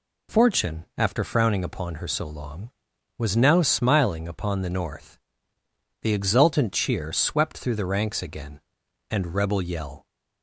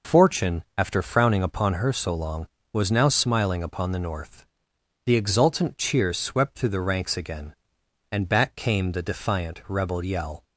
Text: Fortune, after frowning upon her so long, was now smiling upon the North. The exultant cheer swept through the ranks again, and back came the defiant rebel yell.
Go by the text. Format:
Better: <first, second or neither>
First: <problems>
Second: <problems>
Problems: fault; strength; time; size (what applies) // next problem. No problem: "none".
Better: second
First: skips "back came the defiant"; at 9.3 s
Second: none